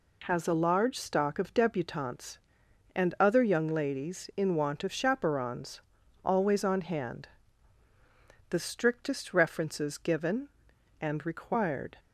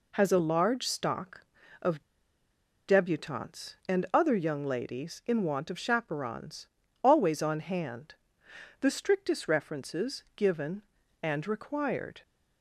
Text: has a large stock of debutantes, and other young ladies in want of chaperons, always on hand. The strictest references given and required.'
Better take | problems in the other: first | pauses between "of" and "debutantes"; noticeable; at 2.0 s; 0.85 s long

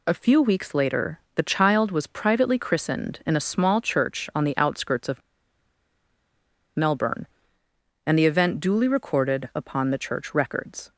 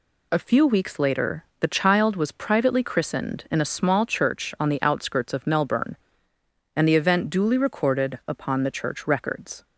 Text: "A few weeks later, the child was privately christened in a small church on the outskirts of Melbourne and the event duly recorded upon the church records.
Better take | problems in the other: second | pauses between "of" and "Melbourne"; strong; at 5.2 s; 1.5 s long

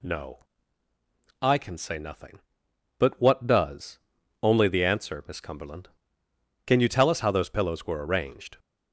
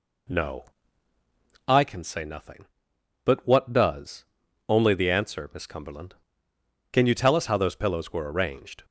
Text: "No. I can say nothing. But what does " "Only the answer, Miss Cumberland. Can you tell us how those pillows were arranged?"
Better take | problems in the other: first | starts louder than the rest; slight; until 1.9 s; 2.5 dB

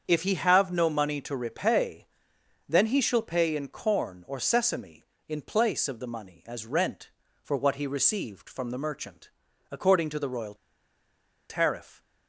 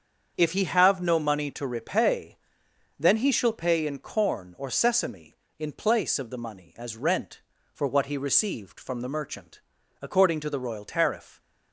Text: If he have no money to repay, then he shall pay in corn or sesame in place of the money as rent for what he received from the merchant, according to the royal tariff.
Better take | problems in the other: second | starts louder than the rest; strong; until 1.0 s; 7 dB; strong in the second // pauses between "royal" and "tariff"; noticeable; at 10.5 s; 0.94 s long

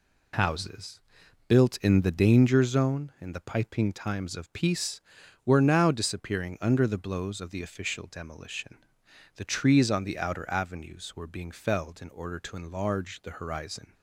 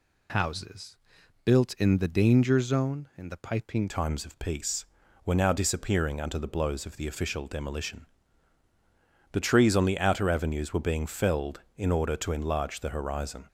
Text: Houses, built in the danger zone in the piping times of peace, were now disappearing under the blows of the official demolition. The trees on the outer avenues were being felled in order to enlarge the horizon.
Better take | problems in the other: first | changes voice at "times"; from 3.8 s on; 9.6 s long

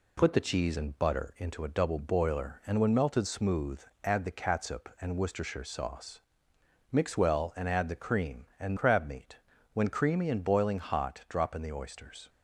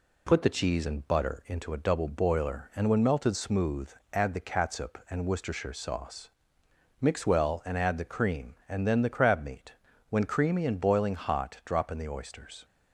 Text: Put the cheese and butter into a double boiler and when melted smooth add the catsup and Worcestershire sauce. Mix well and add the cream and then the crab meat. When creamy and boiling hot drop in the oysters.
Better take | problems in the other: second | pauses between "smooth" and "add"; slight; at 3.8 s; 0.20 s long; slight in the second // skips "then the"; at 8.7 s

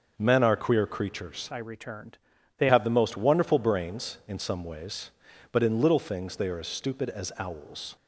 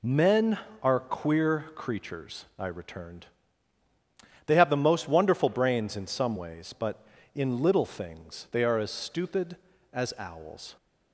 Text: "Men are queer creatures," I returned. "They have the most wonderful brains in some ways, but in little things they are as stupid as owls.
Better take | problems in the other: second | starts louder than the rest; until 1.1 s; 6.5 dB // changes voice from "I" to "They"; from 1.4 to 2.6 s; 1.2 s long

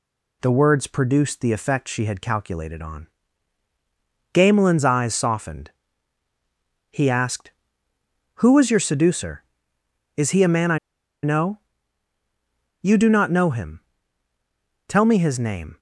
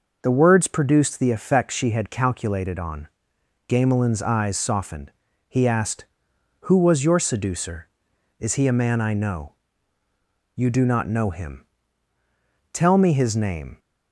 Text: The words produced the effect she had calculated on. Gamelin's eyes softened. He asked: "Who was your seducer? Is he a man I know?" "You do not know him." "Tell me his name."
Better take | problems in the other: second | pauses between "I" and "know"; at 10.7 s; 0.45 s long

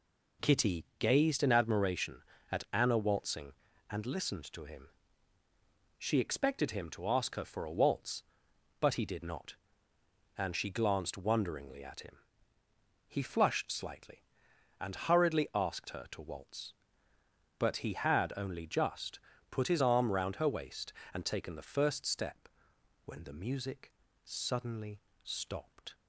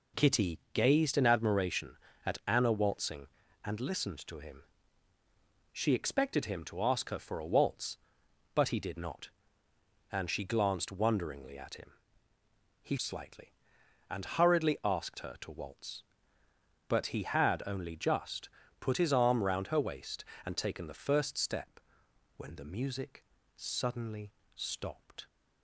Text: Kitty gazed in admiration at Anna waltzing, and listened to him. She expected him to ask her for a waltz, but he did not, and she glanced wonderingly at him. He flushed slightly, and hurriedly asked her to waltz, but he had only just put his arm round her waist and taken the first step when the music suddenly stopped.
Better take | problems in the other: first | skips "flushed"; at 12.9 s // pauses between "just" and "put"; slight; at 18.4 s; 0.32 s long; slight in the first // pauses between "step" and "when"; noticeable; at 21.7 s; 0.58 s long; noticeable in the first // pauses between "music" and "suddenly"; slight; at 23.2 s; 0.32 s long; slight in the first // pauses between "suddenly" and "stopped"; slight; at 24.3 s; 0.22 s long; slight in the first

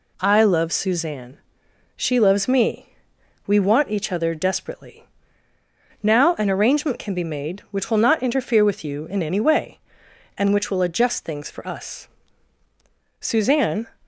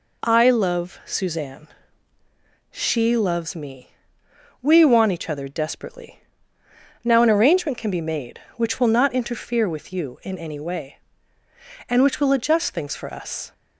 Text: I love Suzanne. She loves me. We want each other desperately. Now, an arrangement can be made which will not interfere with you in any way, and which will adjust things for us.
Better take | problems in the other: second | goes on to say "Suzanne"; noticeable; from 13.1 s on; 0.68 s long

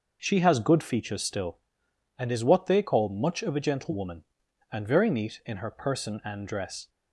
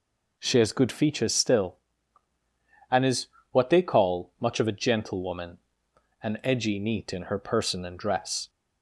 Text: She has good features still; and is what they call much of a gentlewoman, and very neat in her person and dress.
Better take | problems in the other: first | pauses between "is" and "what"; slight; at 3.2 s; 0.24 s long // says "edgy" for "very"; at 6.4 s

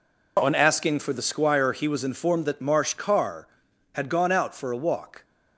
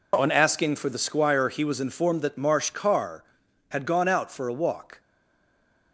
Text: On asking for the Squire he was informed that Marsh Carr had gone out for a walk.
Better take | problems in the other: first | stays silent after the last word; slight; from 5.0 s on; 0.9 s long

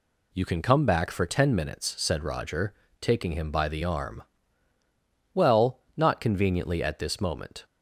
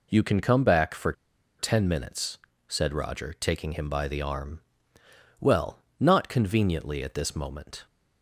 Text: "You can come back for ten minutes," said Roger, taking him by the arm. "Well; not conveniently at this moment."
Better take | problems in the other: first | pauses between "for" and "ten"; noticeable; at 1.1 s; 0.46 s long

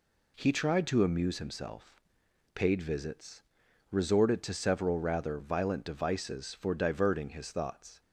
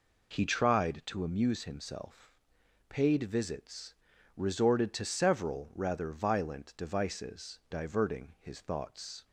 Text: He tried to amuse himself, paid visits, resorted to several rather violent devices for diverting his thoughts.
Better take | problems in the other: first | skips "for"; at 7.6 s

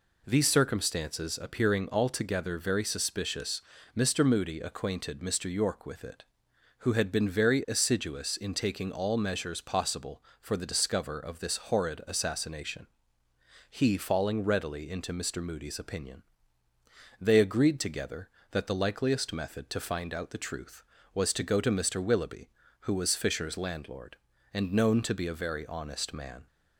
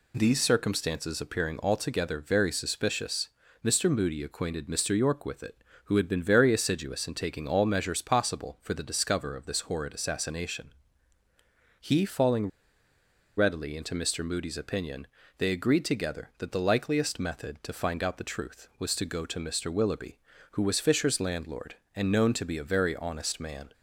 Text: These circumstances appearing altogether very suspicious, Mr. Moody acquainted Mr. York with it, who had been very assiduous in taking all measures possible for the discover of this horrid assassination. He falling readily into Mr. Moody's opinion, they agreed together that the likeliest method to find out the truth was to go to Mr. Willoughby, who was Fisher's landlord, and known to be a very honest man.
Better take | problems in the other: first | pauses between "falling" and "readily"; noticeable; at 12.4 s; 0.89 s long

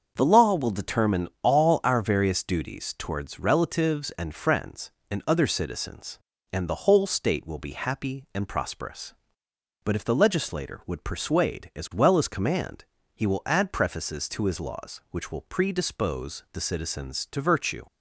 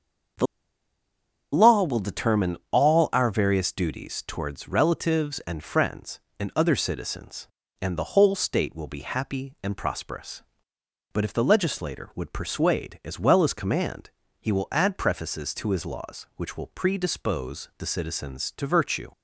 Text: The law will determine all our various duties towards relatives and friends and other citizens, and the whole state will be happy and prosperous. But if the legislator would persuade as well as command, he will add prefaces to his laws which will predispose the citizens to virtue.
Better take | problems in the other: first | starts louder than the rest; until 2.4 s; 6.5 dB; also in the first // pauses between "The" and "law"; at 0.4 s; 1.0 s long

